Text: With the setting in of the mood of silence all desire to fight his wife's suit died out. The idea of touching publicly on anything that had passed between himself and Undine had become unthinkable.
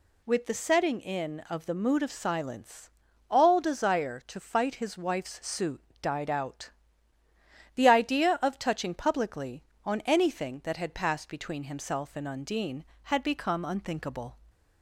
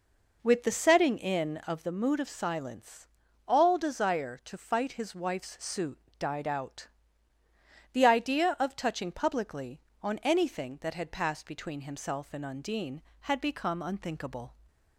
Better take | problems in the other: first | starts louder than the rest; noticeable; until 1.9 s; 4.5 dB // pauses between "silence" and "all"; at 3.0 s; 0.38 s long; also in the first // pauses between "suit" and "died"; slight; at 5.9 s; 0.20 s long; slight in the first

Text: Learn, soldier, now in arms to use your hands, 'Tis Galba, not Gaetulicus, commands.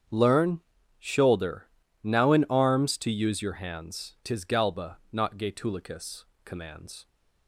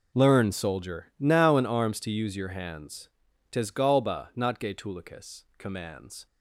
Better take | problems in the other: second | starts louder than the rest; strong; until 1.4 s; 8 dB // says "shoulder" for "soldier"; at 0.9 s

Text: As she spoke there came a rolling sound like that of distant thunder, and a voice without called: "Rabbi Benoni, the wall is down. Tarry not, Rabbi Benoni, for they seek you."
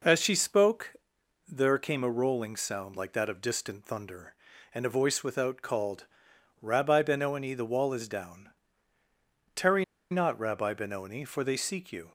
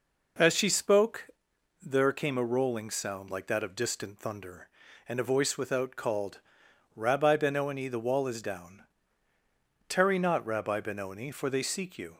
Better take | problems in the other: second | pauses between "spoke" and "there"; noticeable; at 0.9 s; 0.52 s long; noticeable in the second // pauses between "Tarry" and "not"; slight; at 9.8 s; 0.27 s long

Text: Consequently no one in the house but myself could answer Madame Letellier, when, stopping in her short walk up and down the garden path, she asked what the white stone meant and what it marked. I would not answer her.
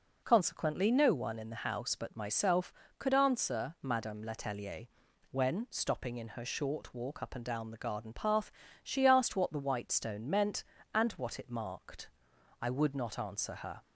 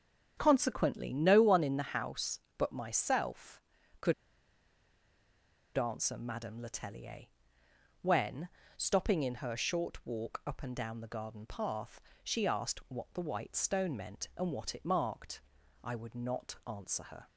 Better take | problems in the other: first | starts louder than the rest; strong; until 1.3 s; 8 dB // pauses between "could" and "answer"; strong; at 4.1 s; 1.6 s long

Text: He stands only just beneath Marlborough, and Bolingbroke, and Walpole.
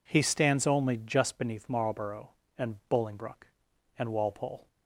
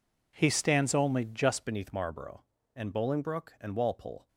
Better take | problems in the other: first | changes voice at "beneath"; from 1.6 s on; 2.6 s long

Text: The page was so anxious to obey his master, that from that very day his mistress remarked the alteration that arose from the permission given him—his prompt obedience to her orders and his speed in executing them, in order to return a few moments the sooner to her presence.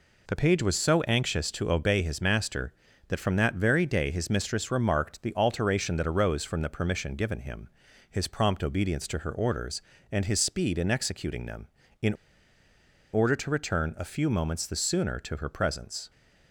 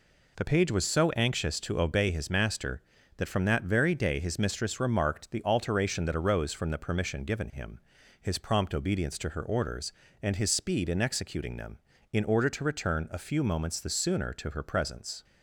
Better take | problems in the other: second | pauses between "in" and "order"; at 12.1 s; 1.0 s long

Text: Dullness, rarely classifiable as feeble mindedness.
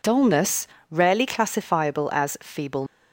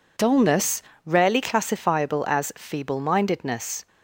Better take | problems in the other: second | stops before "mindedness"; at 2.8 s

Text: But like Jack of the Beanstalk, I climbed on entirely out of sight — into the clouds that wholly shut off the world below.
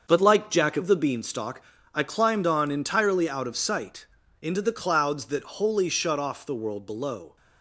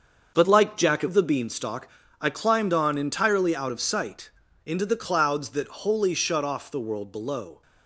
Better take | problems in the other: neither | starts louder than the rest; the same in both

